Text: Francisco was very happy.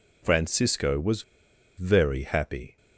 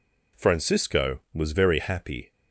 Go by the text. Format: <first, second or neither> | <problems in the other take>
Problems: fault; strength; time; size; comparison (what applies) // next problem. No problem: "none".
second | pauses between "was" and "very"; noticeable; at 1.2 s; 0.55 s long